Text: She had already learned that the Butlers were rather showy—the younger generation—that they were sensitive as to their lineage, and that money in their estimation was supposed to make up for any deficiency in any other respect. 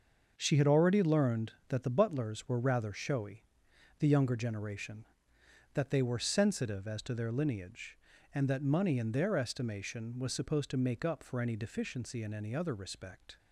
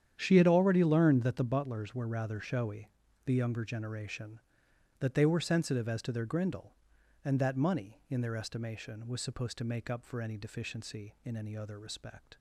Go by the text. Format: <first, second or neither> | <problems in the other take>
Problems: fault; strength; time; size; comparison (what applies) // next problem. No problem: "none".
first | starts louder than the rest; strong; until 1.1 s; 9 dB; also in the first // says "grindle" for "lineage"; at 6.2 s